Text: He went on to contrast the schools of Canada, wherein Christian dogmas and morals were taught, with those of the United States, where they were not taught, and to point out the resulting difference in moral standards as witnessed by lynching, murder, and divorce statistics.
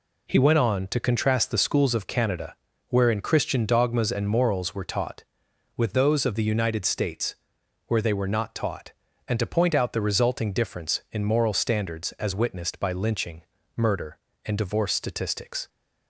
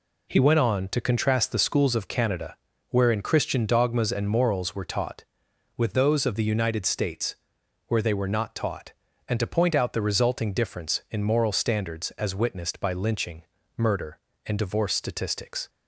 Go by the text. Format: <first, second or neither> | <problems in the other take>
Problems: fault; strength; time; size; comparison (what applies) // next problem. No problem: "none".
neither | none